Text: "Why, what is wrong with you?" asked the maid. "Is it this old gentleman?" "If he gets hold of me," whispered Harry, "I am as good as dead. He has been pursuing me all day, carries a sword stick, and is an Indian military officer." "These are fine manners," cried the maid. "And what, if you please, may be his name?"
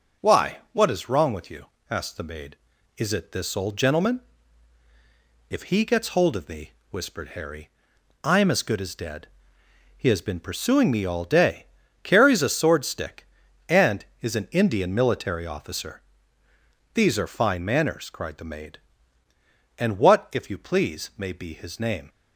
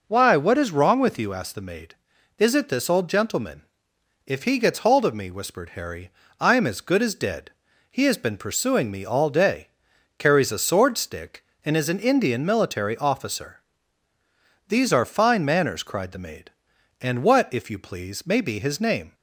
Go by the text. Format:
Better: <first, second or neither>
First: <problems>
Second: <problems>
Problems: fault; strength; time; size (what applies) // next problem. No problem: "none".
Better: neither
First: none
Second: none